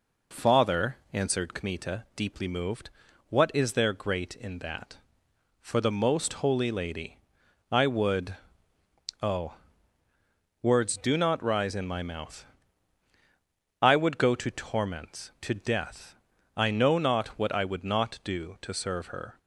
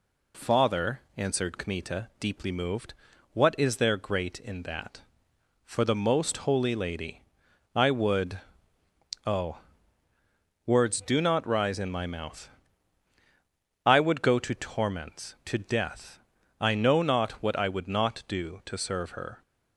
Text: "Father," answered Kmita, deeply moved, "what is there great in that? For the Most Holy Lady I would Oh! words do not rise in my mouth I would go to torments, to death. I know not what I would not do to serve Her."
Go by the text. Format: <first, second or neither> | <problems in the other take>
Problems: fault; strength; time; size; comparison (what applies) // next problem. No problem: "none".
second | starts louder than the rest; noticeable; until 1.4 s; 4 dB // pauses between "Lady" and "I"; noticeable; at 7.1 s; 0.50 s long; noticeable in the second // pauses between "would" and "Oh"; noticeable; at 8.3 s; 0.84 s long; noticeable in the second // pauses between "mouth" and "I"; strong; at 12.4 s; 1.3 s long; strong in the second